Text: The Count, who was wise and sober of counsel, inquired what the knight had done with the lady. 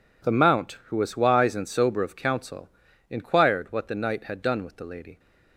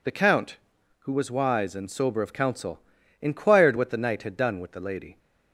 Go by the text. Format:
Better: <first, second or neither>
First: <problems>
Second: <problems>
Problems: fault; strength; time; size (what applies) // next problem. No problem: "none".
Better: second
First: says "Mount" for "Count"; at 0.3 s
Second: none